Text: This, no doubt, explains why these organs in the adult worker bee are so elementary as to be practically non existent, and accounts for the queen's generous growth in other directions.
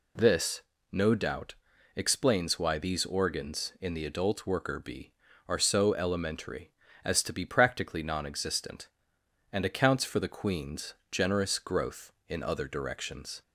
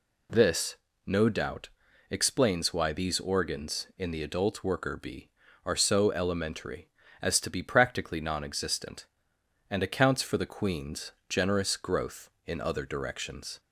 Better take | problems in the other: neither | pauses between "queen's" and "generous"; slight; the same in both

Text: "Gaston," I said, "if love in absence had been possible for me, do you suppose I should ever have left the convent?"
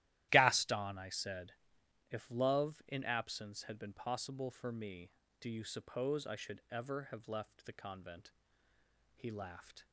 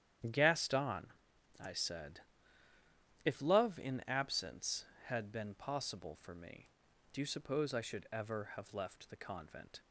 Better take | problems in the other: second | starts louder than the rest; strong; until 1.3 s; 14.5 dB; strong in the second // goes on to say "He laughed"; noticeable; from 9.1 s on; 0.70 s long

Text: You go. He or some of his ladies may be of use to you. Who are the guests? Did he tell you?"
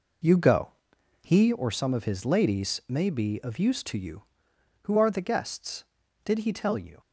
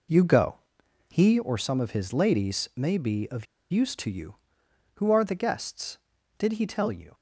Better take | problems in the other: first | pauses between "of" and "use"; slight; at 3.4 s; 0.25 s long

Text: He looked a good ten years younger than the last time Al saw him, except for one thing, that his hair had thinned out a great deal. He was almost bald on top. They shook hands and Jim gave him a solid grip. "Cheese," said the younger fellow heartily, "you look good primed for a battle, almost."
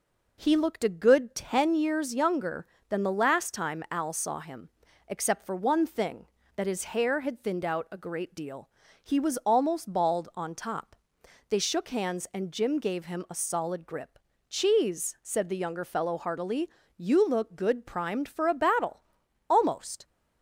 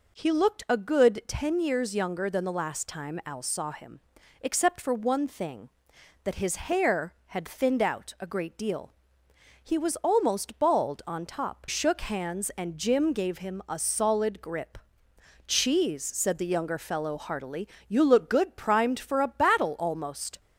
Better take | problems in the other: first | skips "They"; at 11.6 s

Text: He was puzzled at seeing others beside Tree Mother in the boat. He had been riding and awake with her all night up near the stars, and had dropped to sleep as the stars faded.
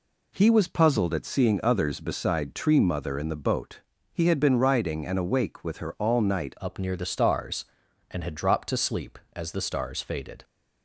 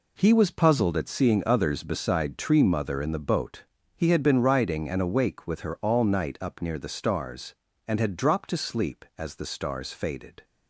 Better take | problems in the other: second | changes voice at "up"; from 6.6 s on; 3.8 s long

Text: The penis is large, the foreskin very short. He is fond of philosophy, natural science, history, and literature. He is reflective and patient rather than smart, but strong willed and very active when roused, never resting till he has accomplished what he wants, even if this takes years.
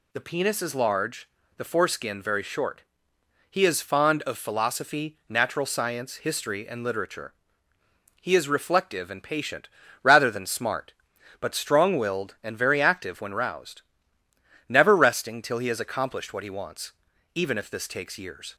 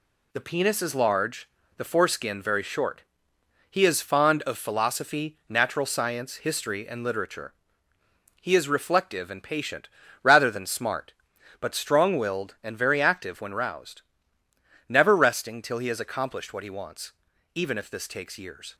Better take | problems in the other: first | gets quieter; noticeable; throughout; 5 dB // pauses between "patient" and "rather"; slight; at 9.8 s; 0.34 s long; slight in the first

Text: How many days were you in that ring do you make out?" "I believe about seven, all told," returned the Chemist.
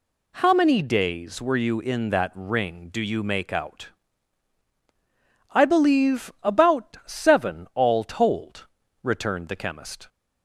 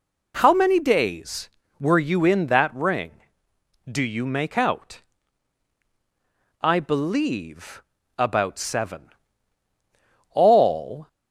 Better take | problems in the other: first | pauses between "believe" and "about"; slight; at 7.8 s; 0.36 s long // stops before "told returned the Chemist"; at 11.0 s

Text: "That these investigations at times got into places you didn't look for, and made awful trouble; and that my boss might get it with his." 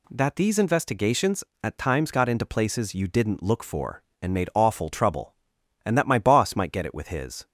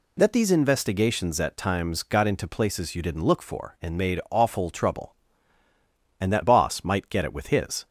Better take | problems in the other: first | skips "my"; at 6.4 s

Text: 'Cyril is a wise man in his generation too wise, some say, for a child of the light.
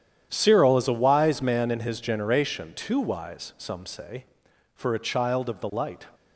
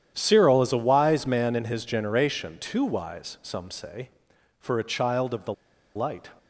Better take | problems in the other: first | starts louder than the rest; strong; until 1.1 s; 10 dB; strong in the first // pauses between "the" and "light"; at 5.5 s; 0.41 s long

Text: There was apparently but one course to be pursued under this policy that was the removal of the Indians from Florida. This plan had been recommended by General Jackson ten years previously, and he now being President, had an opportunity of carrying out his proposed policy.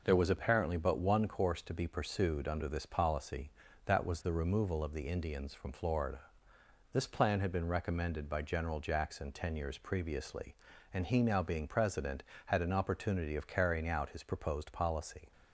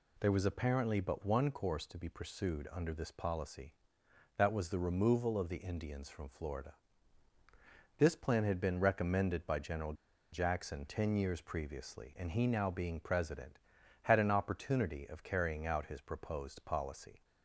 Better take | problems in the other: first | pauses between "General" and "Jackson"; at 9.9 s; 0.38 s long

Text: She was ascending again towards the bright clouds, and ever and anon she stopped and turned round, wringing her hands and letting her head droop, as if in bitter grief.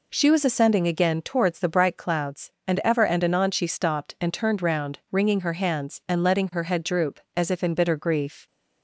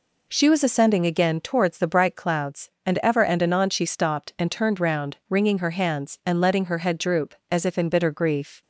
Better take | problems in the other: neither | none

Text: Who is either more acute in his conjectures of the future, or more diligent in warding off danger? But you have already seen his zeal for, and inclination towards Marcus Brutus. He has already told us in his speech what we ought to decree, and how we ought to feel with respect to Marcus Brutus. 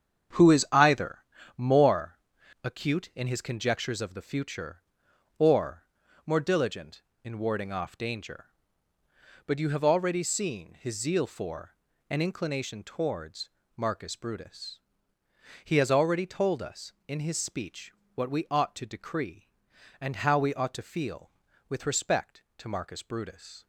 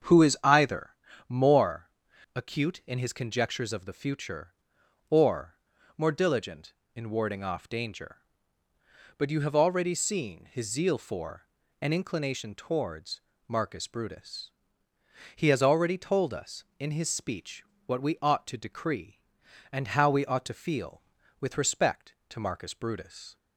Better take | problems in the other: second | gets quieter; strong; throughout; 8.5 dB // starts louder than the rest; strong; until 1.7 s; 8 dB; strong in the second // pauses between "either" and "more"; slight; at 1.2 s; 0.34 s long; slight in the second // pauses between "more" and "acute"; noticeable; at 2.1 s; 0.46 s long; noticeable in the second // pauses between "or" and "more"; at 5.8 s; 0.42 s long; also in the second // pauses between "towards" and "Marcus"; slight; at 13.4 s; 0.26 s long; slight in the second // pauses between "speech" and "what"; slight; at 17.9 s; 0.24 s long; slight in the second

